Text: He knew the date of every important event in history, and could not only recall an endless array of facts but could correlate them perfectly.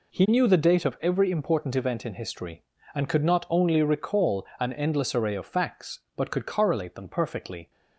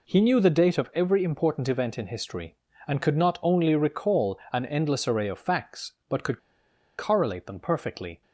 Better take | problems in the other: first | pauses between "recall" and "an"; slight; at 4.3 s; 0.16 s long; slight in the first // pauses between "could" and "correlate"; noticeable; at 6.3 s; 0.61 s long

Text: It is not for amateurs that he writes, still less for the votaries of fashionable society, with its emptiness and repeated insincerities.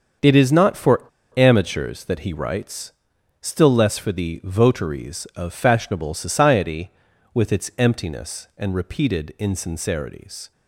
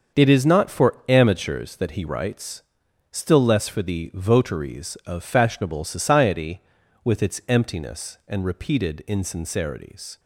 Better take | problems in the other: second | starts louder than the rest; until 1.5 s; 6.5 dB; also in the second // pauses between "for" and "amateurs"; slight; at 1.0 s; 0.28 s long

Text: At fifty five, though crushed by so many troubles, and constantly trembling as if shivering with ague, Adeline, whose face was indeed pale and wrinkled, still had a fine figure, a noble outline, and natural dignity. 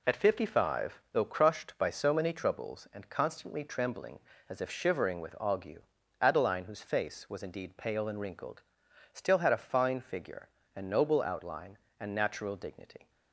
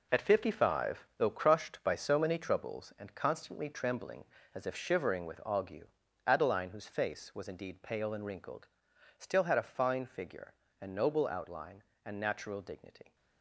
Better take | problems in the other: first | gets quieter; strong; throughout; 9 dB

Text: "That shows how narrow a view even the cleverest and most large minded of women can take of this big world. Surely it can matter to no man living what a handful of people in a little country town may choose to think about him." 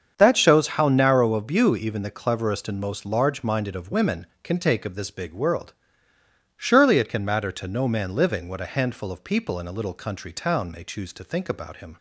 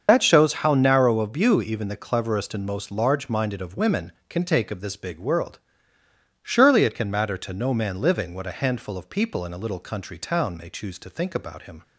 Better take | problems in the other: first | loses the start of "That"; at 0.0 s; 65 ms // starts louder than the rest; until 1.0 s; 7 dB; also in the first

